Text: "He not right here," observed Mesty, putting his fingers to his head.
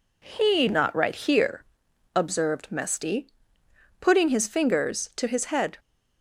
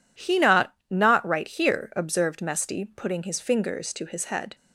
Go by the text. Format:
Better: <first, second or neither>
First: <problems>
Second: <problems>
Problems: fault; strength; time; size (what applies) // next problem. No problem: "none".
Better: first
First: none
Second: says "not" twice; at 0.8 s